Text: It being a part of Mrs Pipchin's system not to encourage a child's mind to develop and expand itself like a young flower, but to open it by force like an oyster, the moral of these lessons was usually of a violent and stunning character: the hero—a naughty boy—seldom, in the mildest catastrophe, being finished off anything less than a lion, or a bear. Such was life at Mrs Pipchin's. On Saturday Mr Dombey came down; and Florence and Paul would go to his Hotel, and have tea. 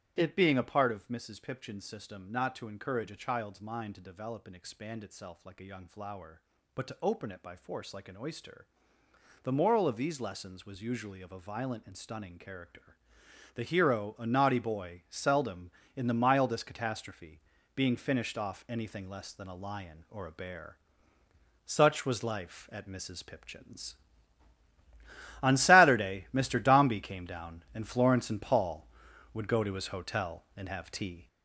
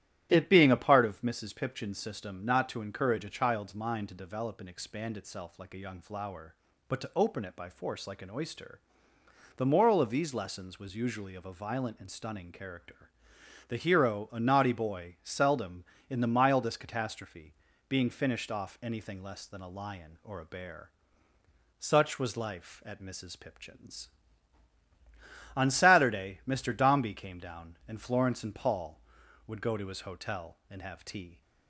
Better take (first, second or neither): second